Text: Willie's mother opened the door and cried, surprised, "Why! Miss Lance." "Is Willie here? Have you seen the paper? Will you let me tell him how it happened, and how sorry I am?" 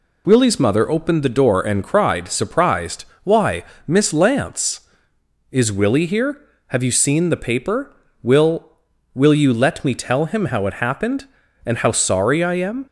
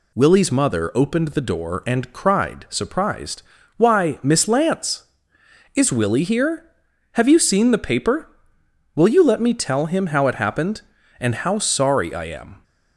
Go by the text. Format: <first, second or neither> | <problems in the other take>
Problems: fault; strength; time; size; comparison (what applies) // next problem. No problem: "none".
second | says "Will" twice; at 9.1 s